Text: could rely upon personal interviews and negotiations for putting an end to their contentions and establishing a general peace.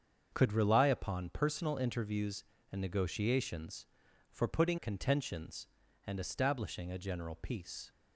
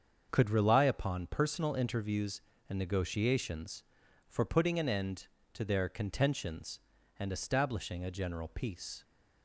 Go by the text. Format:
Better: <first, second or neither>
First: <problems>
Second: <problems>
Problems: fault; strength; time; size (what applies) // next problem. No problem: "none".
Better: second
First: starts louder than the rest; until 1.3 s; 7 dB // skips "an end to their"; at 4.7 s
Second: starts louder than the rest; until 1.3 s; 7 dB